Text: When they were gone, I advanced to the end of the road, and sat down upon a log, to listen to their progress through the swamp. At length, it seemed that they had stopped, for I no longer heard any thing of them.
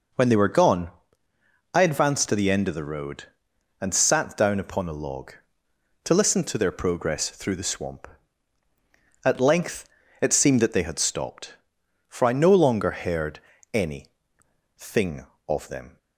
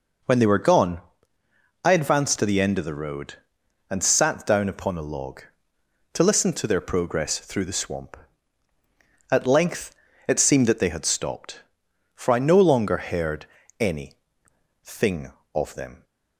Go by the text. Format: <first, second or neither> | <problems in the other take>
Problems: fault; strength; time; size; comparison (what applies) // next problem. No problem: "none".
neither | pauses between "heard" and "any"; slight; the same in both // pauses between "any" and "thing"; noticeable; the same in both